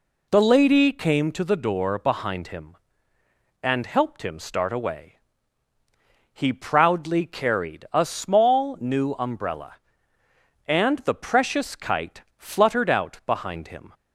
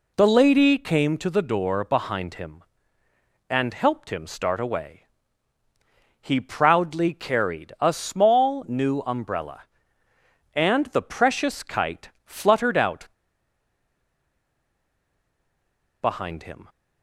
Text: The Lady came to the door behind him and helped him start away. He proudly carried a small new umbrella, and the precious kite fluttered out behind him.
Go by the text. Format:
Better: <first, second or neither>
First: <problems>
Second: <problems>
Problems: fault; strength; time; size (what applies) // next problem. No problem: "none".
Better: first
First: pauses between "kite" and "fluttered"; slight; at 12.2 s; 0.16 s long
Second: pauses between "kite" and "fluttered"; slight; at 12.0 s; 0.16 s long // pauses between "out" and "behind"; strong; at 13.0 s; 2.9 s long